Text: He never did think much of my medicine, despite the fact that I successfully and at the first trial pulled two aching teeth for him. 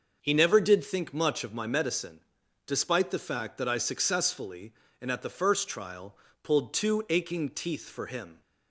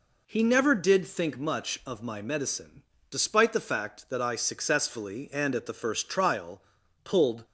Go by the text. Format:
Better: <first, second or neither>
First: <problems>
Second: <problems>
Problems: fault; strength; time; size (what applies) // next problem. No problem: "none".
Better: first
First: pauses between "trial" and "pulled"; slight; at 6.1 s; 0.28 s long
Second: pauses between "trial" and "pulled"; at 6.6 s; 0.42 s long // stops before "two aching teeth for him"; at 7.4 s